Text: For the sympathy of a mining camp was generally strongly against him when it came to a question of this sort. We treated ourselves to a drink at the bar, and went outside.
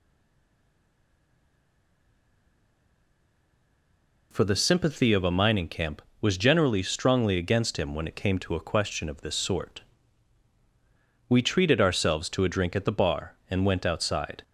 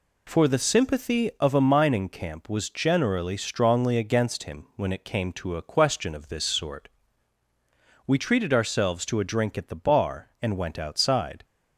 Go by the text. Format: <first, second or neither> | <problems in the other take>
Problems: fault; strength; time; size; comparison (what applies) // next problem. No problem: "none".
second | stays silent before the first word; strong; until 4.3 s; 4.3 s long